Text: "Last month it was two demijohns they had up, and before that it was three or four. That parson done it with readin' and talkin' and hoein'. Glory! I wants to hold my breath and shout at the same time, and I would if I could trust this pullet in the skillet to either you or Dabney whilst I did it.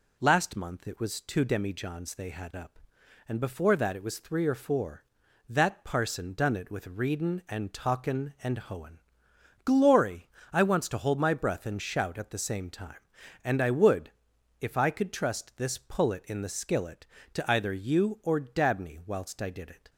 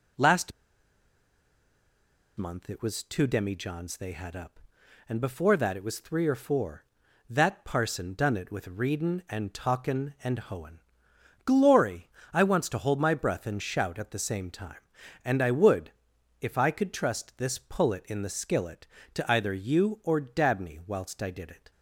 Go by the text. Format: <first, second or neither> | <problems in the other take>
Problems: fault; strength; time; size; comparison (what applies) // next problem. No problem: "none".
first | pauses between "Last" and "month"; strong; at 0.5 s; 1.8 s long // pauses between "would" and "if"; noticeable; at 15.9 s; 0.52 s long; noticeable in the first